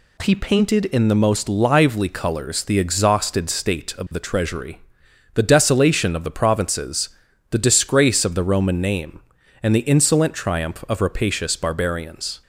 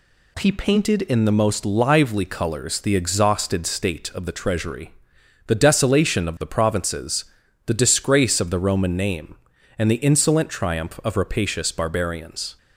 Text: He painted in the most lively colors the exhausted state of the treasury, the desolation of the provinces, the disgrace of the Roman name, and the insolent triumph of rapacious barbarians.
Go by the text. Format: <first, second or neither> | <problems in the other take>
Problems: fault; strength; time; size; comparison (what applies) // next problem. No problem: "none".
neither | none